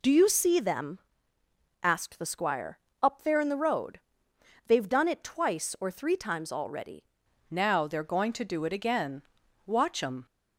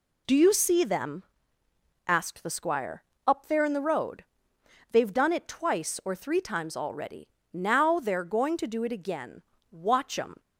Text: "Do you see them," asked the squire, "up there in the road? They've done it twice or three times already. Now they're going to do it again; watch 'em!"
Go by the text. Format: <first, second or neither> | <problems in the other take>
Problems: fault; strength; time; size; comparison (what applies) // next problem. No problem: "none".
second | changes voice at "Now"; from 7.4 s on; 2.8 s long